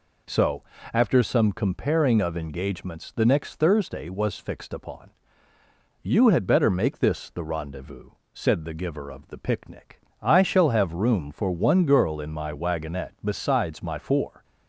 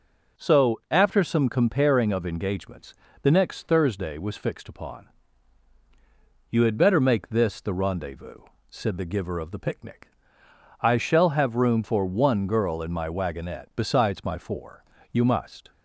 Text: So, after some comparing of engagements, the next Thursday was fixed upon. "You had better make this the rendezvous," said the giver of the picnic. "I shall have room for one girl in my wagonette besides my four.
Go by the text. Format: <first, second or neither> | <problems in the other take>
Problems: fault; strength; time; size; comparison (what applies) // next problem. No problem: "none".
first | goes on to say "You must"; from 15.1 s on; 0.60 s long